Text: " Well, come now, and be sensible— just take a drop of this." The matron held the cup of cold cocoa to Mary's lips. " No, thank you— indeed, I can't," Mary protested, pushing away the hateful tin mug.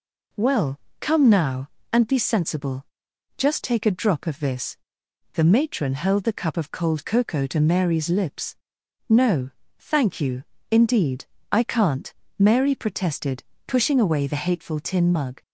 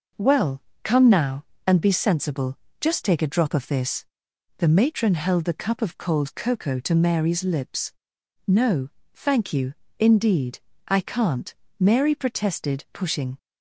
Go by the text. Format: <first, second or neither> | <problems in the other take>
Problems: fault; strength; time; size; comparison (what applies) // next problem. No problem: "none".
first | stops before "away the hateful tin mug"; at 13.3 s